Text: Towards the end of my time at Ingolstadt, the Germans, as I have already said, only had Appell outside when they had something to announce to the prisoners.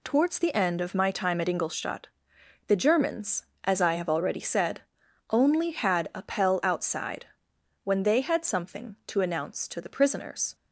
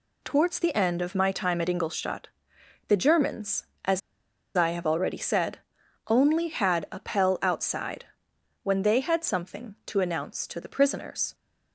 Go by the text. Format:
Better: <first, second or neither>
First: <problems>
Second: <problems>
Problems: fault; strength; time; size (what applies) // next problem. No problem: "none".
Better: first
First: pauses between "outside" and "when"; noticeable; at 7.2 s; 0.56 s long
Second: pauses between "as" and "I"; noticeable; at 4.0 s; 0.56 s long // pauses between "outside" and "when"; noticeable; at 8.0 s; 0.56 s long